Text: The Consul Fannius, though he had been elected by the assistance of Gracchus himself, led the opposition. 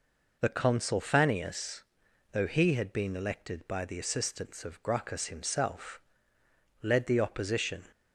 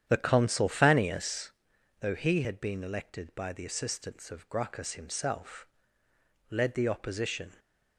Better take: first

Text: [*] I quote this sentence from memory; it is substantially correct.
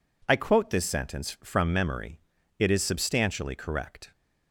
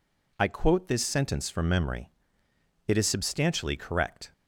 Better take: neither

